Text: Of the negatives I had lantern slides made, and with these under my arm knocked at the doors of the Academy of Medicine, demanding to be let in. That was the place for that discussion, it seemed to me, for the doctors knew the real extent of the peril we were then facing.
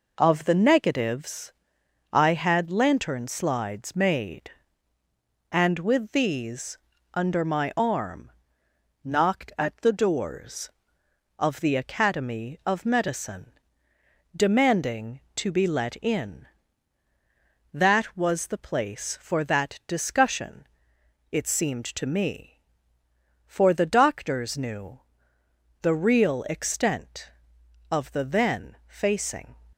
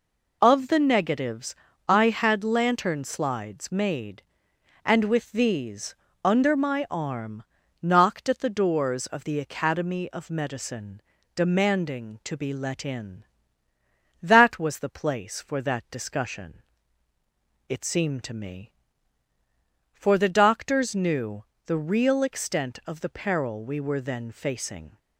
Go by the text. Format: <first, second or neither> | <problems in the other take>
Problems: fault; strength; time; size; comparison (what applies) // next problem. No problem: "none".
second | pauses between "negatives" and "I"; noticeable; at 1.5 s; 0.60 s long; slight in the second // pauses between "these" and "under"; slight; at 6.7 s; 0.36 s long; slight in the second // pauses between "arm" and "knocked"; noticeable; at 8.3 s; 0.72 s long; also in the second // pauses between "knew" and "the"; noticeable; at 25.0 s; 0.82 s long; slight in the second // skips "peril we were"; at 28.2 s